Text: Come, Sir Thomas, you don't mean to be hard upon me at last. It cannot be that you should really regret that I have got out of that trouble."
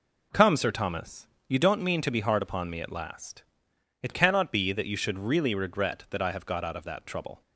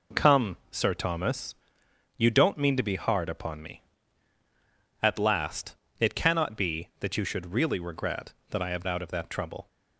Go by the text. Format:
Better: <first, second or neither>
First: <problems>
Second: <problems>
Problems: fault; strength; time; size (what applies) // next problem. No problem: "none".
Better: first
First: none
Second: skips "got"; at 8.8 s